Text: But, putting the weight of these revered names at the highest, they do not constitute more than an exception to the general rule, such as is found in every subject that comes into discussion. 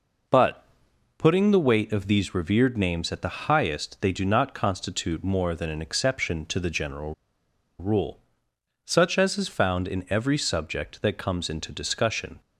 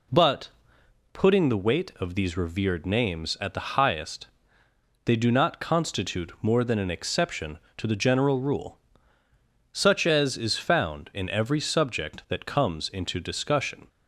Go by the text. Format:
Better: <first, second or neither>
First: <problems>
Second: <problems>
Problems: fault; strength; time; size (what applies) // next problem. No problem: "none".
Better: second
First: pauses between "general" and "rule"; noticeable; at 7.1 s; 0.65 s long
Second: none